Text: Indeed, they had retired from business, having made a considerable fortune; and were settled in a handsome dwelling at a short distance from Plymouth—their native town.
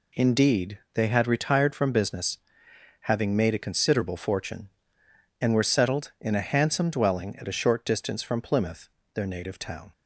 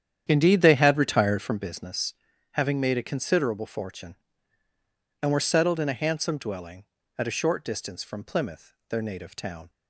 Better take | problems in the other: first | starts louder than the rest; strong; until 1.5 s; 9 dB

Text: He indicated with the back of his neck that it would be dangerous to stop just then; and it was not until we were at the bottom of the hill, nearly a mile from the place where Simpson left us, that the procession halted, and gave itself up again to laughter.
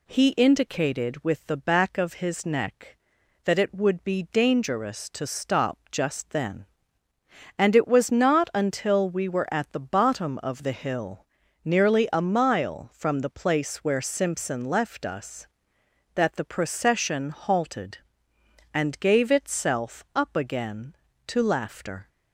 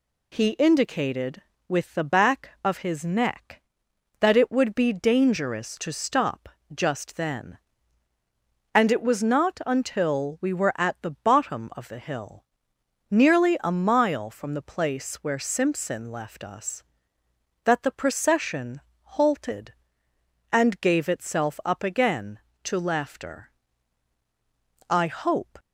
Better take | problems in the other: first | pauses between "stop" and "just"; slight; at 6.4 s; 0.24 s long // pauses between "procession" and "halted"; slight; at 18.8 s; 0.22 s long // goes on to say "I hope"; noticeable; from 24.8 s on; 0.70 s long

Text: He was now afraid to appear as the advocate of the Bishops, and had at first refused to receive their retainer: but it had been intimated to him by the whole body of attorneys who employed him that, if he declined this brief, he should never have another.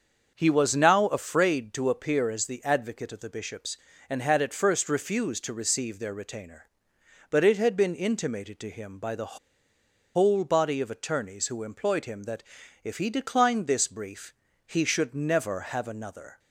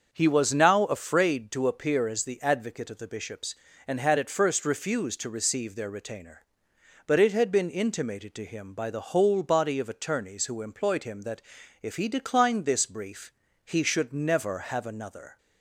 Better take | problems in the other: second | starts louder than the rest; until 1.3 s; 6.5 dB; also in the second // pauses between "the" and "whole"; noticeable; at 9.3 s; 0.77 s long

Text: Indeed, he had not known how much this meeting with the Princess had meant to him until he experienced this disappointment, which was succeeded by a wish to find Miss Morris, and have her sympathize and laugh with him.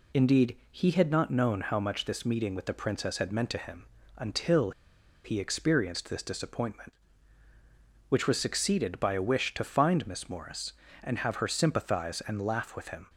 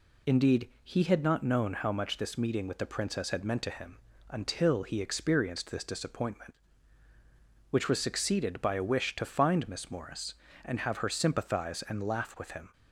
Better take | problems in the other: second | pauses between "him" and "until"; slight; at 3.8 s; 0.32 s long; slight in the second // pauses between "until" and "he"; noticeable; at 4.7 s; 0.53 s long

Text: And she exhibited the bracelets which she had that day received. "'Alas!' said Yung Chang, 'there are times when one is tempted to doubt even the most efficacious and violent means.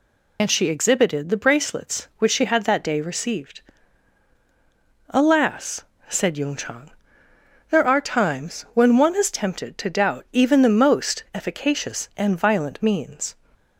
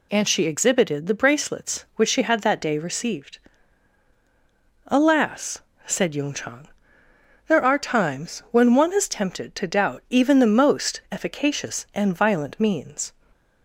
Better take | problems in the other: second | loses the start of "And"; at 0.3 s; 70 ms

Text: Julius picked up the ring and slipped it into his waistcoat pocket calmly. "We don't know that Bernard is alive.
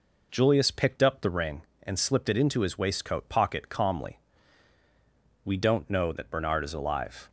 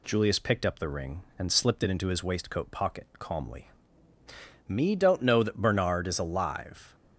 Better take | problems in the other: first | says "Me" for "We"; at 4.6 s

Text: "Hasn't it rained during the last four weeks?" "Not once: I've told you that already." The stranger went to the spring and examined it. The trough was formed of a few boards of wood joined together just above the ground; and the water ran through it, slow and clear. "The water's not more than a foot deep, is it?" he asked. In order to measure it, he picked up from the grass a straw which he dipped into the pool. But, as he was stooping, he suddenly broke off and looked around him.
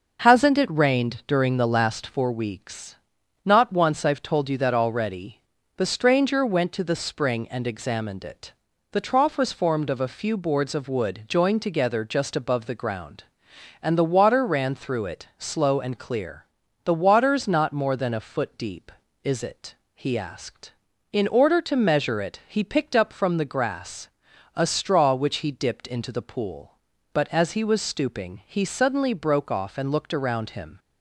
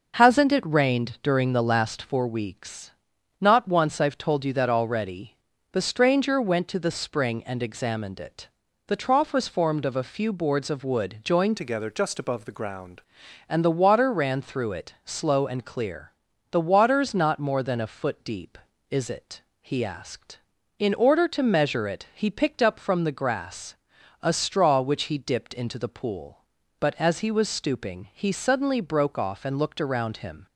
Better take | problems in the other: first | changes voice from "together" to "ground"; from 11.5 to 13.0 s; 1.5 s long // pauses between "grass" and "a"; at 23.7 s; 0.44 s long; also in the first

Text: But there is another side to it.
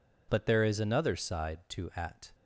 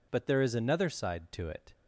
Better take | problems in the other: second | says "at" for "it"; at 1.9 s

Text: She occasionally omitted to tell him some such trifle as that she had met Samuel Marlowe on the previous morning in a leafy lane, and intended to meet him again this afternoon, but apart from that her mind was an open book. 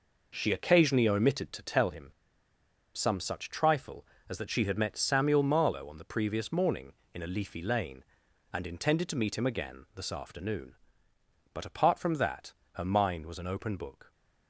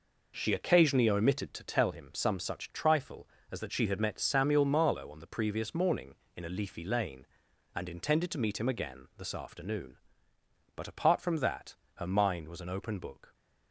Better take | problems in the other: second | pauses between "him" and "some"; noticeable; at 2.0 s; 0.85 s long // pauses between "that" and "her"; slight; at 12.5 s; 0.22 s long; slight in the second

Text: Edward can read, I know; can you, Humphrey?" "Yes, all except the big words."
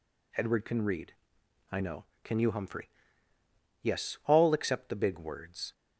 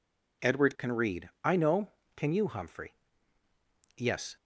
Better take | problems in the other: first | stops before "all except the big words"; at 4.3 s

